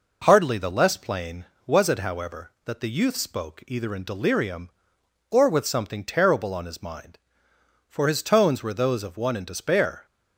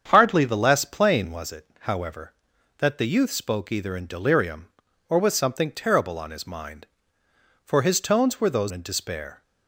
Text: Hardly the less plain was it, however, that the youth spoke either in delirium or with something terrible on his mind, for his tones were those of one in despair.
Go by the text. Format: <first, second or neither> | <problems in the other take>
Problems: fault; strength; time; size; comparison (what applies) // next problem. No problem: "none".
first | starts louder than the rest; strong; until 1.1 s; 7.5 dB // skips "of one"; at 8.7 s